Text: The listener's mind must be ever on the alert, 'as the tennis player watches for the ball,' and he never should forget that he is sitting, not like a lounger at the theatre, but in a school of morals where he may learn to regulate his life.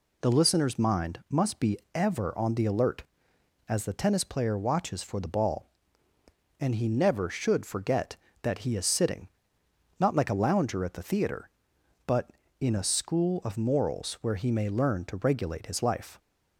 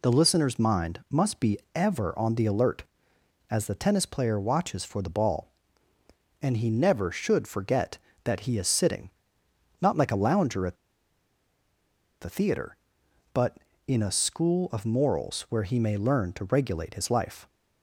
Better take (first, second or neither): first